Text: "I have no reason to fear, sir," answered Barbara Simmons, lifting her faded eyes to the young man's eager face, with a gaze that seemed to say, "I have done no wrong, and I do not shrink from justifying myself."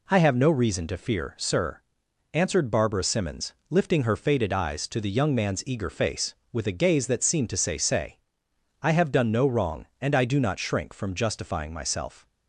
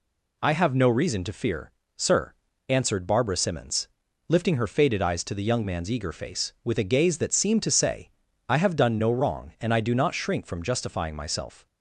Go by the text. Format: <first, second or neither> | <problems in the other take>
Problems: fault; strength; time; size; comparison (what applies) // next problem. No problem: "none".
second | says "say" twice; at 7.7 s